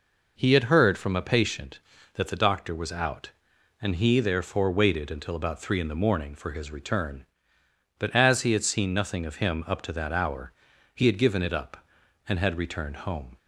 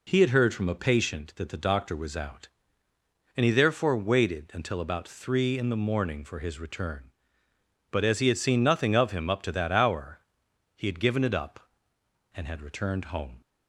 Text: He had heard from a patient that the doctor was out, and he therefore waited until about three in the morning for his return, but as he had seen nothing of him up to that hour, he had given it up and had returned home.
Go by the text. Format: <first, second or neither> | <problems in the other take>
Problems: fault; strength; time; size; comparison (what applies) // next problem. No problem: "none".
neither | none